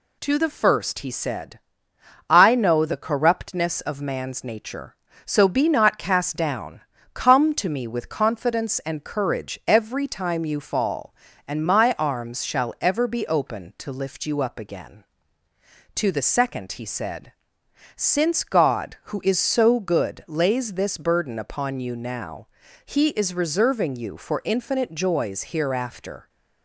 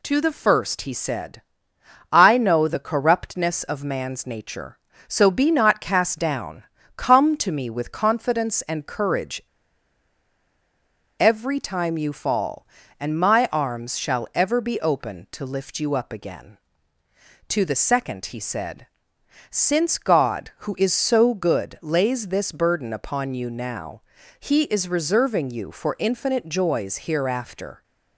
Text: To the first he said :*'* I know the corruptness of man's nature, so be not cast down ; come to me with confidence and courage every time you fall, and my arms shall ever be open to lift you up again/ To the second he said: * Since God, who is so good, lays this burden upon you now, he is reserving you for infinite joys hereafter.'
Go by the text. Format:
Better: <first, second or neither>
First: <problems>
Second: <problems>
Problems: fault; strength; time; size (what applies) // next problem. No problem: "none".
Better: first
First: none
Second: pauses between "courage" and "every"; strong; at 9.4 s; 1.7 s long